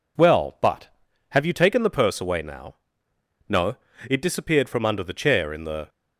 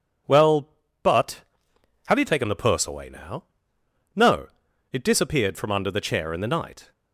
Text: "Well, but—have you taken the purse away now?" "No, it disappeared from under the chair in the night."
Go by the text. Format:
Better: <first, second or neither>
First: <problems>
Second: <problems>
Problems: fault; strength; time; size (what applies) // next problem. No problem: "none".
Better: second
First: stops before "night"; at 5.8 s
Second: none